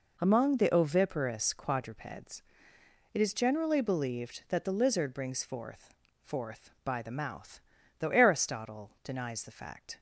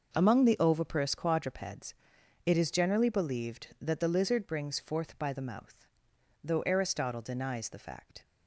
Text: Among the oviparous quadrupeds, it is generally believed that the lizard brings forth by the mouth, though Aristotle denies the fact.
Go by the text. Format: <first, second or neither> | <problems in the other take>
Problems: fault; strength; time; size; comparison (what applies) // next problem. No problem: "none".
second | says "forth" twice; at 6.2 s